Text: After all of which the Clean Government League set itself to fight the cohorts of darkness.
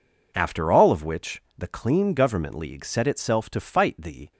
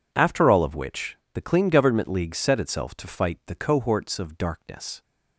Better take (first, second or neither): second